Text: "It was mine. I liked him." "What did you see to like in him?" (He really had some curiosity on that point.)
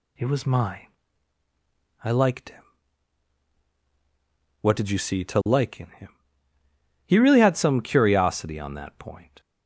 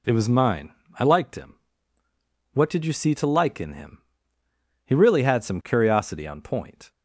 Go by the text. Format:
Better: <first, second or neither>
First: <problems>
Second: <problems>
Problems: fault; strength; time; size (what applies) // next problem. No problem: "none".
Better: first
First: none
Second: skips "that"; at 6.4 s